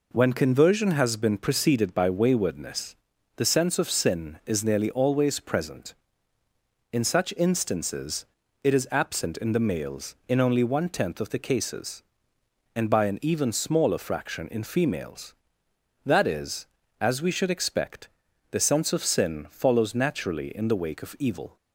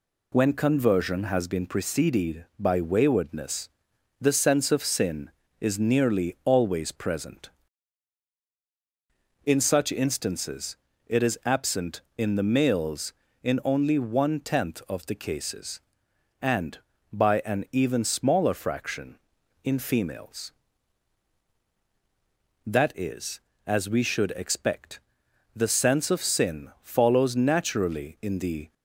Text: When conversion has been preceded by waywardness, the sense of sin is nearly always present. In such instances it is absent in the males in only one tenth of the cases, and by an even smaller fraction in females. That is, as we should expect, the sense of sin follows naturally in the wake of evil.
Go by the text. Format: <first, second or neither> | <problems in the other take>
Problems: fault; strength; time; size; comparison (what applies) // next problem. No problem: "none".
first | pauses between "instances" and "it"; slight; at 10.7 s; 0.30 s long; slight in the first // stops before "wake of evil"; at 28.7 s